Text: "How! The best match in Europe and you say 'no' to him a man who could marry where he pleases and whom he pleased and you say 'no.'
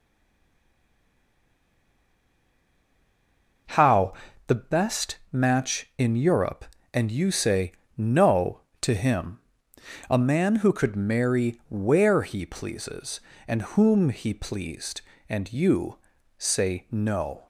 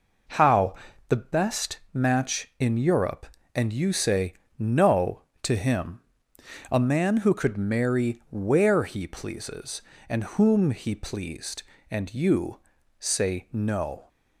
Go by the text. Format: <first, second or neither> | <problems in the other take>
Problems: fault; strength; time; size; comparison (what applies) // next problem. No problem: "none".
second | stays silent before the first word; strong; until 3.6 s; 3.6 s long // pauses between "best" and "match"; slight; at 5.1 s; 0.16 s long; slight in the second // pauses between "say" and "no"; slight; at 7.7 s; 0.24 s long; slight in the second // pauses between "him" and "a"; noticeable; at 9.3 s; 0.70 s long; noticeable in the second // pauses between "you" and "say"; at 15.9 s; 0.40 s long; also in the second